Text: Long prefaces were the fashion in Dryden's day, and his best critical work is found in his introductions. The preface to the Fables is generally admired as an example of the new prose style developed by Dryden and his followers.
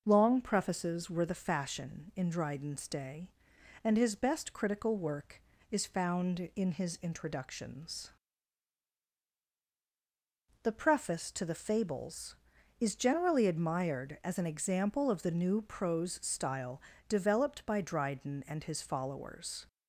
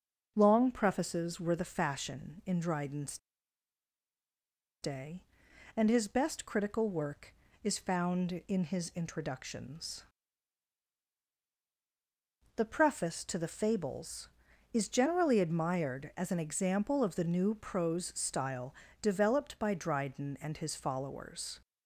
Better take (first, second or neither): first